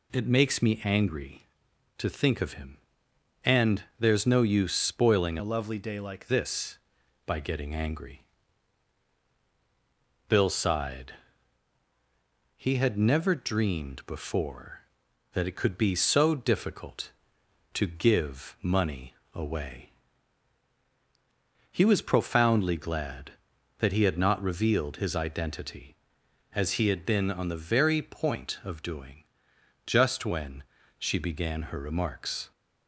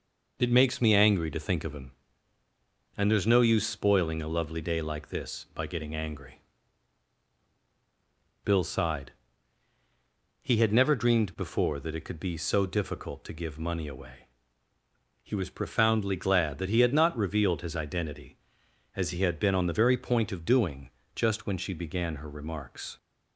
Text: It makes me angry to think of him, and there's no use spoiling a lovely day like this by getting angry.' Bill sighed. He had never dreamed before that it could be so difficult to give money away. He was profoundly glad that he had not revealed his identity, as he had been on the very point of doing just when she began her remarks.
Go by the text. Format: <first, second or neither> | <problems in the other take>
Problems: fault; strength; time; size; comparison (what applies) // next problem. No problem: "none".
second | changes voice from "a" to "like"; from 5.3 to 6.2 s; 0.9 s long // pauses between "money" and "away"; slight; at 19.1 s; 0.22 s long // pauses between "doing" and "just"; noticeable; at 29.1 s; 0.72 s long; slight in the second // pauses between "when" and "she"; slight; at 30.6 s; 0.36 s long